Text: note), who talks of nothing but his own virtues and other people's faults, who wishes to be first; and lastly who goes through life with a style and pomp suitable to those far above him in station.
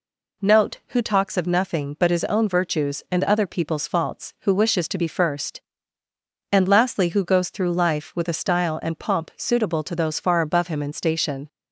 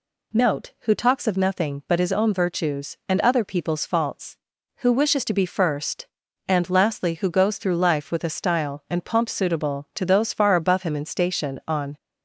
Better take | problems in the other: first | goes on to say "On"; slight; from 11.6 s on; 0.30 s long

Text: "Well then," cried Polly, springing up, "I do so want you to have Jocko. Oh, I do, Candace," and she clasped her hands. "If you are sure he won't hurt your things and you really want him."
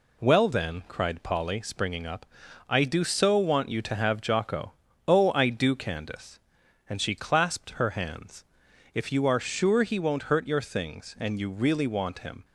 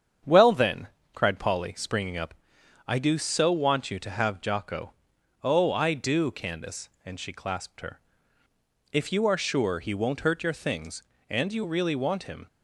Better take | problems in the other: first | starts louder than the rest; strong; until 1.5 s; 8 dB // skips "hands"; at 8.4 s

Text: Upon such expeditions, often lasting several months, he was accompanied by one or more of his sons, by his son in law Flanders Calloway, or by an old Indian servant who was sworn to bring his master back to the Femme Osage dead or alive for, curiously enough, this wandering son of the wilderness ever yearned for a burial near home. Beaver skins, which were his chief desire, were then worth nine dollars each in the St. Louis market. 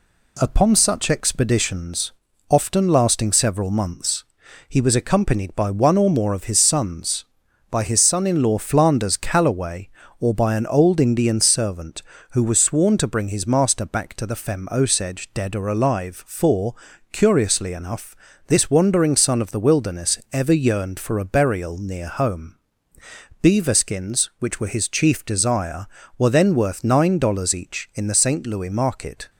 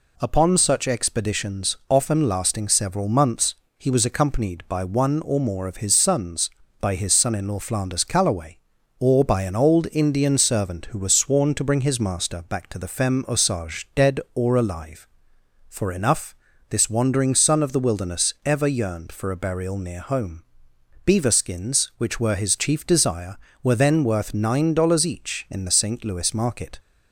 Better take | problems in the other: first | skips "curiously"; at 15.9 s

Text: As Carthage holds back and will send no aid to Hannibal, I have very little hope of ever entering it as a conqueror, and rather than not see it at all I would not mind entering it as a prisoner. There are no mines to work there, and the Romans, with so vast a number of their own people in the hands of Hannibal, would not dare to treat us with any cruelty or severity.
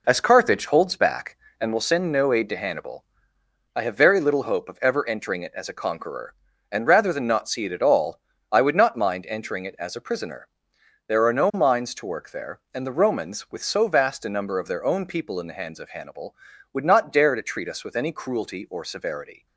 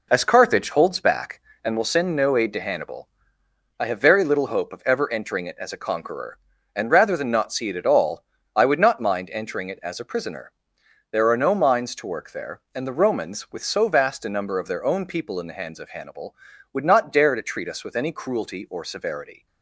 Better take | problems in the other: neither | pauses between "all" and "I"; slight; the same in both

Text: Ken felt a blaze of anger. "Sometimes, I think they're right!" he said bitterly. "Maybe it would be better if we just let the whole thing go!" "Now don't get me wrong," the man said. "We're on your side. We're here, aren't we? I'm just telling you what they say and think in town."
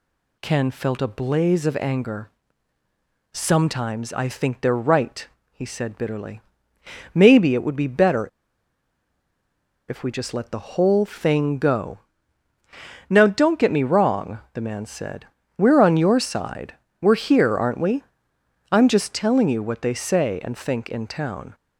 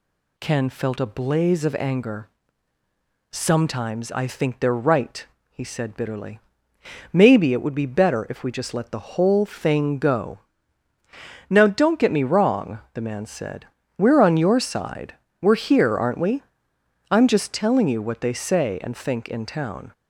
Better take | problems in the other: second | pauses between "better" and "if"; strong; at 8.2 s; 1.6 s long

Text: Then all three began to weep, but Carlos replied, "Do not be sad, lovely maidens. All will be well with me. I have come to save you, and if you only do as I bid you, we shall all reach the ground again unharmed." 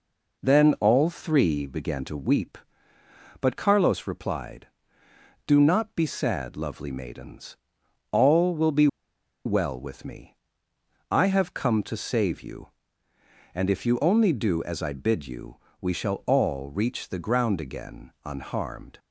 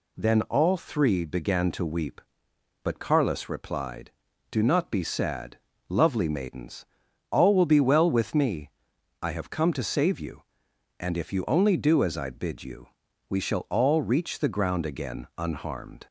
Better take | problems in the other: second | pauses between "be" and "well"; noticeable; at 8.8 s; 0.58 s long

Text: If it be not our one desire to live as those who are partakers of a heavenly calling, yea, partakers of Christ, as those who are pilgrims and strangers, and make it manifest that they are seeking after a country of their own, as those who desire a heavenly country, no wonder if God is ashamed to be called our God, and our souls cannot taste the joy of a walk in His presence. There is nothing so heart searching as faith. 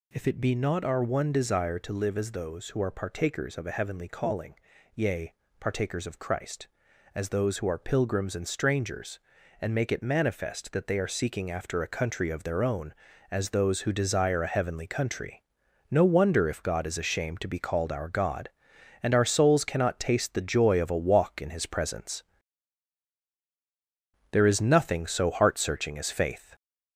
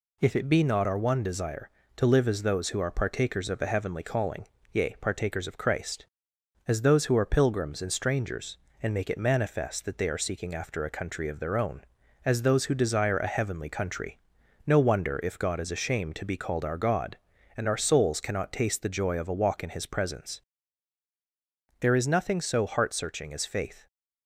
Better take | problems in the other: second | gets louder; noticeable; throughout; 4 dB

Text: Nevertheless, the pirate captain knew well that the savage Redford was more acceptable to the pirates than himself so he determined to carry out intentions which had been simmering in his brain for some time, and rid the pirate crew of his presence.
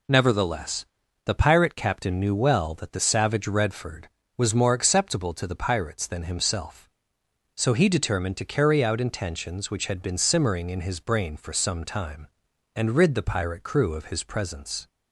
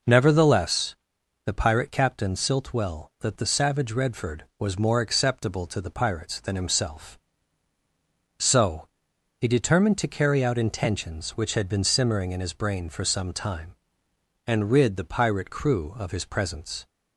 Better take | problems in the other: first | says "silt" for "knew"; at 2.3 s // pauses between "so" and "he"; noticeable; at 8.8 s; 0.50 s long

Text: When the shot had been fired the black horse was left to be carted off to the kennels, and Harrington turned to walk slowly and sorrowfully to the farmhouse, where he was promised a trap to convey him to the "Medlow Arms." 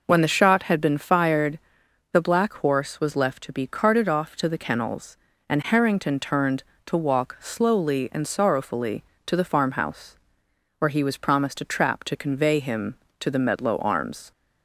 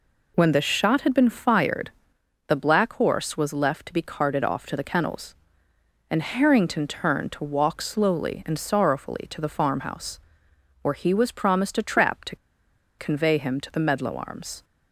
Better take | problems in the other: first | pauses between "fired" and "the"; noticeable; at 1.9 s; 0.56 s long; noticeable in the first // pauses between "to" and "convey"; noticeable; at 12.3 s; 0.63 s long

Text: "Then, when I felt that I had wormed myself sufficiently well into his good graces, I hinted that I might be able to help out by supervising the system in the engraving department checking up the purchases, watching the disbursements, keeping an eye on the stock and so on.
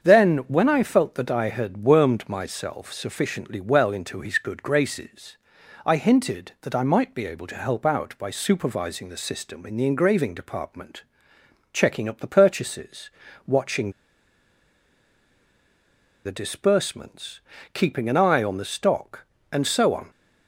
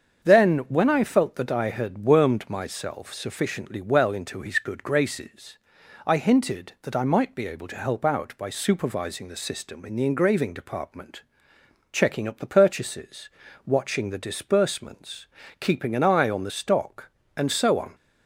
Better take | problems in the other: second | starts louder than the rest; strong; until 1.1 s; 7 dB; strong in the second // pauses between "department" and "checking"; noticeable; at 11.0 s; 0.70 s long; noticeable in the second // pauses between "watching" and "the"; strong; at 13.9 s; 2.3 s long

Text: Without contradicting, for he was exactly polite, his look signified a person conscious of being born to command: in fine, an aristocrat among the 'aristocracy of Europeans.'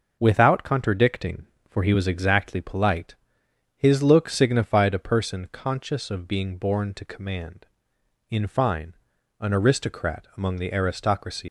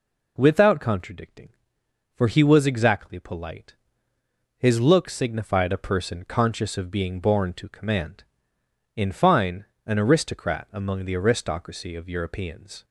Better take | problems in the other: second | stops before "of Europeans"; at 11.4 s

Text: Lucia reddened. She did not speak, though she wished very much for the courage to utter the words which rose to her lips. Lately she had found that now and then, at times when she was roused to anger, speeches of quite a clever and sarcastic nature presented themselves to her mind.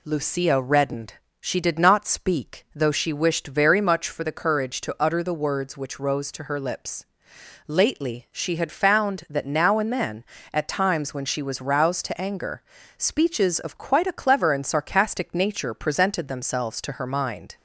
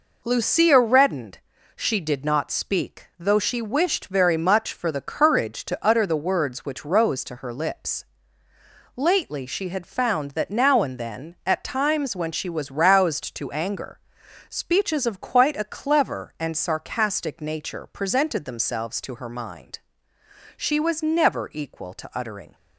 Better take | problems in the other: first | goes on to say "She was never equal to uttering"; strong; from 20.5 s on; 1.9 s long

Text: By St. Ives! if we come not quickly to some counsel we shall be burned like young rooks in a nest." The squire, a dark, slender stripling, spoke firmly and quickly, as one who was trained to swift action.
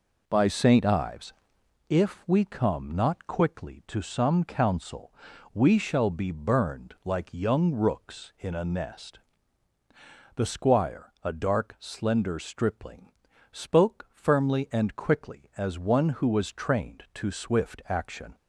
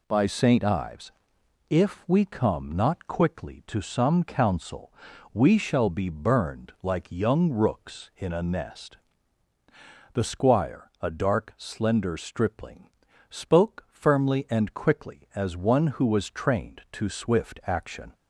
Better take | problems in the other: second | starts louder than the rest; noticeable; until 1.7 s; 4.5 dB // pauses between "counsel" and "we"; at 5.1 s; 0.42 s long; also in the second

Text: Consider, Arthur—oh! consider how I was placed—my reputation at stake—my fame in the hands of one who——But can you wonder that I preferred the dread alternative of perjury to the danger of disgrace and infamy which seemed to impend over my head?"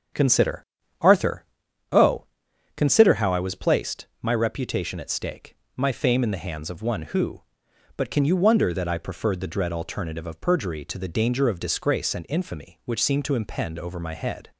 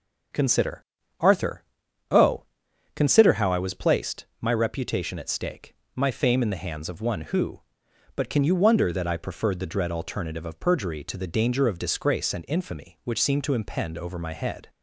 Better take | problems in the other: second | starts louder than the rest; until 1.6 s; 6.5 dB

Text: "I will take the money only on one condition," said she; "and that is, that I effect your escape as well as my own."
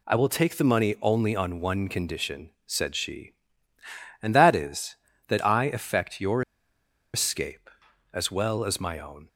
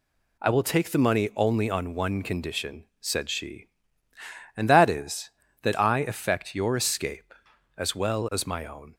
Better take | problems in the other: second | pauses between "your" and "escape"; noticeable; at 6.4 s; 0.72 s long

